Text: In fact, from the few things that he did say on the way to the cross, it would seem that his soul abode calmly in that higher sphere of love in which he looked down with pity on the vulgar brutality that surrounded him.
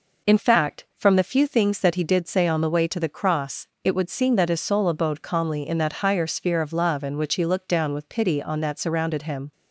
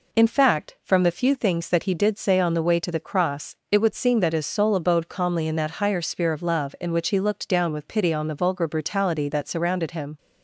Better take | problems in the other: second | skips "the vulgar brutality"; at 8.5 s

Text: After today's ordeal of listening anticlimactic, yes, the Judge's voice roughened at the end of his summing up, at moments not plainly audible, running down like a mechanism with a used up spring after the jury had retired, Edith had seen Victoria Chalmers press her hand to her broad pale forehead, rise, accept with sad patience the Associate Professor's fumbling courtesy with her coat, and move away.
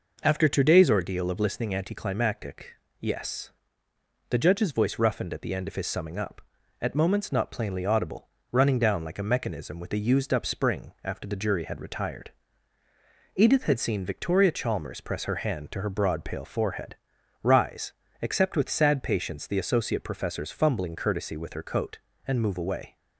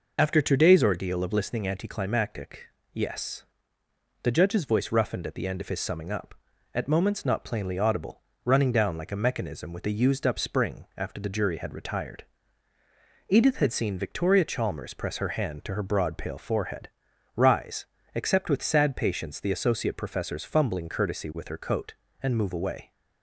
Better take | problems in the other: first | loses the start of "After"; at 0.1 s; 65 ms

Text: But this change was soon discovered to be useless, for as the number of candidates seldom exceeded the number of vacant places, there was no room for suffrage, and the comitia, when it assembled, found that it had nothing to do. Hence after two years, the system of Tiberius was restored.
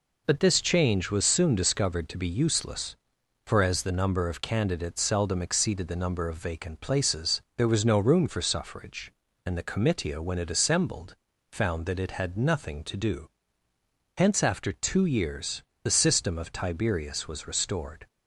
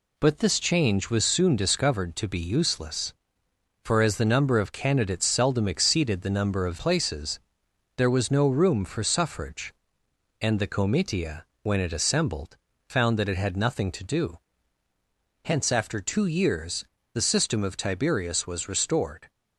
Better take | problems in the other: first | skips "vacant"; at 6.7 s

